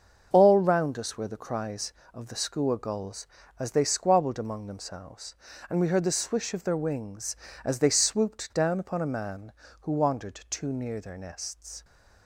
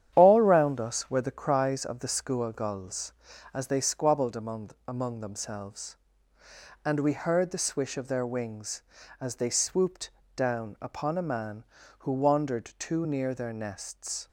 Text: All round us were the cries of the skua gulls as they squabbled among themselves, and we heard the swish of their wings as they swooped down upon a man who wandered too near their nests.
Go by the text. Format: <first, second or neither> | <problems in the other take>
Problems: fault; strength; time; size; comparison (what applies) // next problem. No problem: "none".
first | starts louder than the rest; strong; until 1.1 s; 10 dB; also in the first // says "among" twice; at 4.8 s // pauses between "swooped" and "down"; slight; at 10.1 s; 0.24 s long